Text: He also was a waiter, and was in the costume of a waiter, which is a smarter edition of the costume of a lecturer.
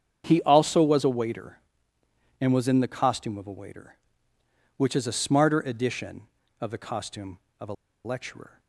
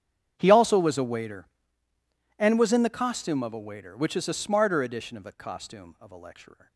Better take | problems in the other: second | starts louder than the rest; strong; until 1.2 s; 7.5 dB; strong in the second // pauses between "a" and "lecturer"; slight; at 7.7 s; 0.31 s long

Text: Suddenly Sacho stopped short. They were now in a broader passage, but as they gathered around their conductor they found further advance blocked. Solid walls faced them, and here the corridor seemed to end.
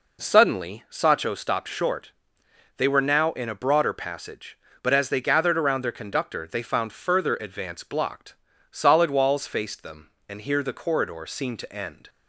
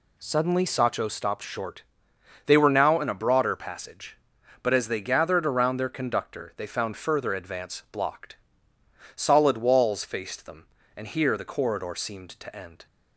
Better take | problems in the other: neither | none

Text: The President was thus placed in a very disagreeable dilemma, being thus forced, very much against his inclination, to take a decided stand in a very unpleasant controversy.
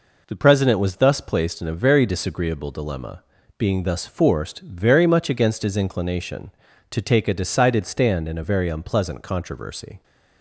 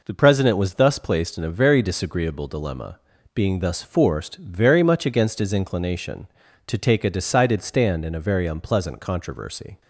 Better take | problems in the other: neither | none

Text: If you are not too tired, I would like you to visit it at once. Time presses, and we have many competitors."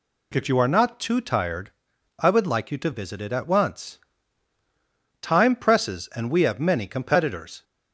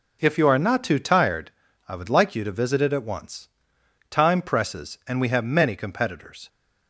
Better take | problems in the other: neither | none

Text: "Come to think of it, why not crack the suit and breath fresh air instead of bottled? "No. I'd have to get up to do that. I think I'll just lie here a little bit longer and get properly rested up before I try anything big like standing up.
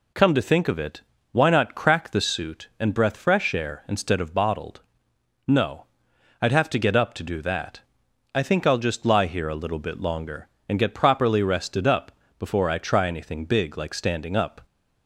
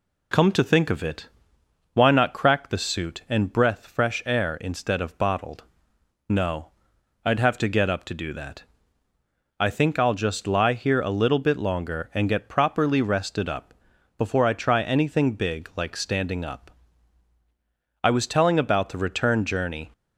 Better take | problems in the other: first | pauses between "up" and "before"; at 13.7 s; 0.42 s long; slight in the first // goes on to say "I was telling about the return journey"; strong; from 18.0 s on; 1.8 s long

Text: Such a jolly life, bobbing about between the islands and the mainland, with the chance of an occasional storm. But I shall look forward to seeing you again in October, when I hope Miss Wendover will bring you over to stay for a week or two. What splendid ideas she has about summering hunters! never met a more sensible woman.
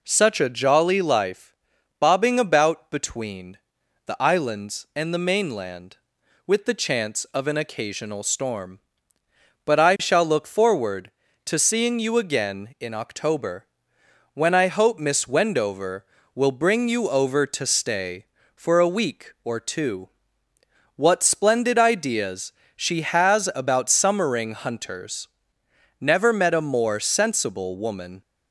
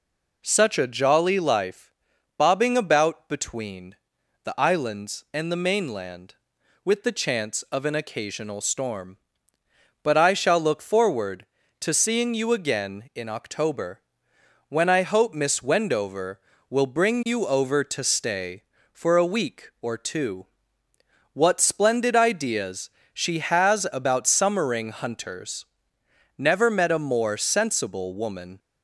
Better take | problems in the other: neither | pauses between "between" and "the"; noticeable; the same in both // pauses between "ideas" and "she"; slight; the same in both

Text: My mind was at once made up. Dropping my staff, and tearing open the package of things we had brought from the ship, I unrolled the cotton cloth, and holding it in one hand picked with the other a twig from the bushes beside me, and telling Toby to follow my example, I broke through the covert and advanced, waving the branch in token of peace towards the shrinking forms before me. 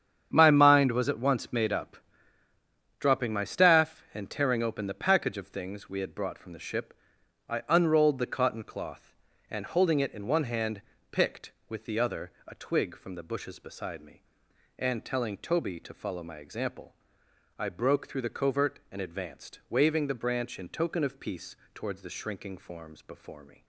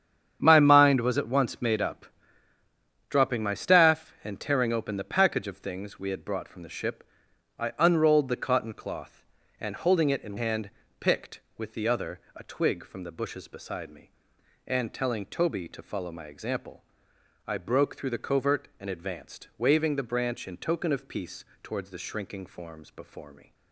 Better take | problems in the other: first | starts louder than the rest; strong; until 1.4 s; 8.5 dB; strong in the first // skips "one"; at 10.3 s // pauses between "hand" and "picked"; slight; at 10.6 s; 0.30 s long; slight in the first // pauses between "other" and "a"; slight; at 12.1 s; 0.16 s long; slight in the first // pauses between "peace" and "towards"; slight; at 21.4 s; 0.18 s long; slight in the first

